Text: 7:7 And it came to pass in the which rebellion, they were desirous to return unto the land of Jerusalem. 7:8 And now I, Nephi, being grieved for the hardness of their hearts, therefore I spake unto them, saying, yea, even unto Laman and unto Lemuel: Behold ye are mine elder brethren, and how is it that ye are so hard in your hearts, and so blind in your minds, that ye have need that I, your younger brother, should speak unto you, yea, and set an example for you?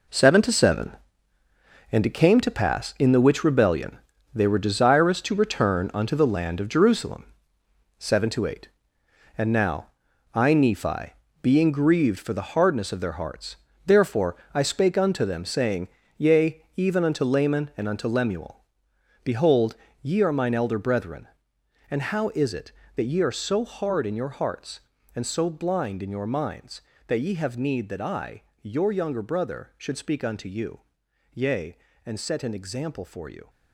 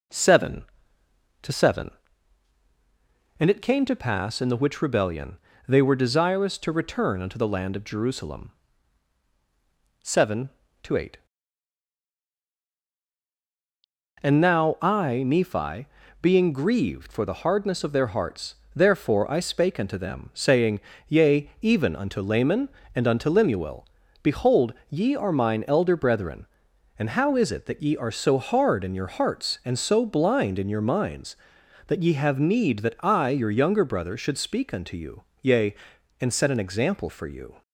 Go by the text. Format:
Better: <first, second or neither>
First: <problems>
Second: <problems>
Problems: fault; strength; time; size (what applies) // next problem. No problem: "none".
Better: second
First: gets quieter; strong; throughout; 11 dB // pauses between "now" and "I"; noticeable; at 9.8 s; 0.46 s long // pauses between "therefore" and "I"; slight; at 14.3 s; 0.18 s long // pauses between "Behold" and "ye"; slight; at 19.7 s; 0.26 s long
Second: pauses between "Behold" and "ye"; slight; at 24.7 s; 0.16 s long